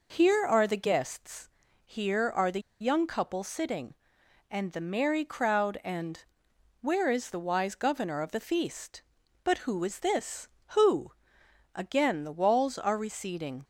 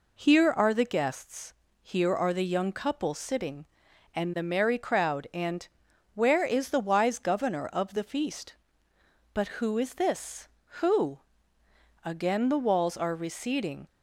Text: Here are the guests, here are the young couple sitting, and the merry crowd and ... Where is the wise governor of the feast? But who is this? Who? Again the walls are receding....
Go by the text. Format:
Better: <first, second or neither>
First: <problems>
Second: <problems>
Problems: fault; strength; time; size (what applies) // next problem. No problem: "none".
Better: second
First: pauses between "the" and "young"; slight; at 2.5 s; 0.21 s long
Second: none